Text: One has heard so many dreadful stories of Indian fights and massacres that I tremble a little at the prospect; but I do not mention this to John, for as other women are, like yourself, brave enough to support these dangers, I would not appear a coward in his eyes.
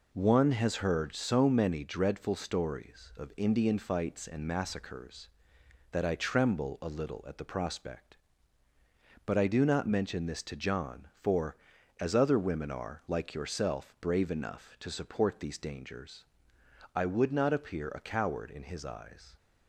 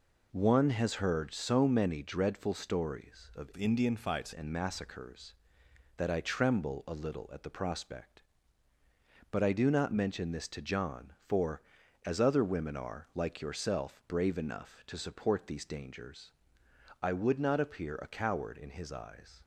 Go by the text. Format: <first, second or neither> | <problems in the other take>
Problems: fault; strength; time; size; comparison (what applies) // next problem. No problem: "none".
first | changes voice from "Indian" to "fights"; from 3.5 to 4.3 s; 0.8 s long